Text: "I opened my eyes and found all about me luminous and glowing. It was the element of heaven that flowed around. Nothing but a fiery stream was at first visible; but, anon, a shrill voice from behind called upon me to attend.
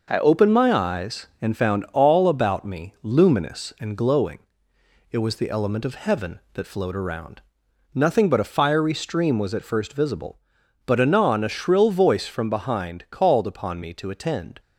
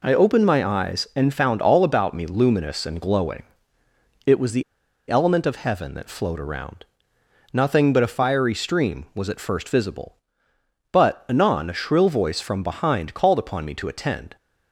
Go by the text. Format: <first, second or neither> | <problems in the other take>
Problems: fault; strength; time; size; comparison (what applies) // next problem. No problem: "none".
first | pauses between "the" and "element"; noticeable; at 4.6 s; 0.46 s long